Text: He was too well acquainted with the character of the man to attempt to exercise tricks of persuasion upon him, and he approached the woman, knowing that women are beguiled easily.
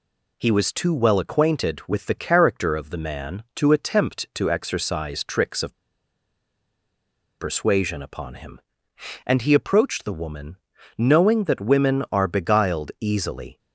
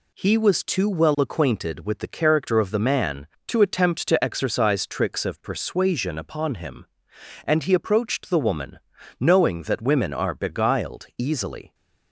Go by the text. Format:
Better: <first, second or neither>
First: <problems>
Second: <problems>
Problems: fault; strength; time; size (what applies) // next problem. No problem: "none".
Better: second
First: pauses between "of" and "persuasion"; strong; at 5.7 s; 1.6 s long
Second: none